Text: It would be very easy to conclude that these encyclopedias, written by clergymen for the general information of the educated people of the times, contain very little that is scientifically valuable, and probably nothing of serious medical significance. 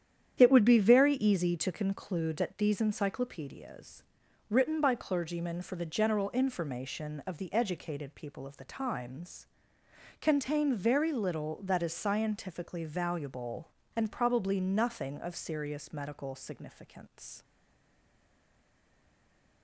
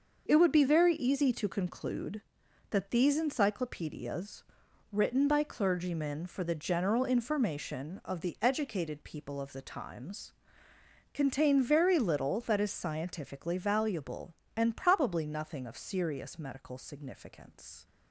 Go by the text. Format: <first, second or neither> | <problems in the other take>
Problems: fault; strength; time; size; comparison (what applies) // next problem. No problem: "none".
second | starts louder than the rest; strong; until 1.4 s; 9.5 dB; noticeable in the second // stays silent after the last word; from 17.4 s on; 2.2 s long